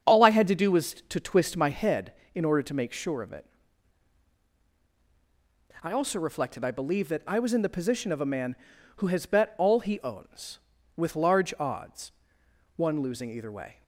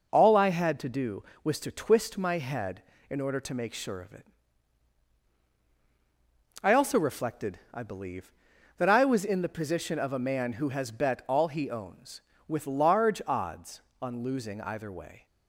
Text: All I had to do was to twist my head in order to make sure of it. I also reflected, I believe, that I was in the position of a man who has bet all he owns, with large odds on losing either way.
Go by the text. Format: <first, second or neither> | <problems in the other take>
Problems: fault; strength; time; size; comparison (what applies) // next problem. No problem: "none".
second | starts louder than the rest; strong; until 1.2 s; 7.5 dB // says "one" for "on"; at 12.7 s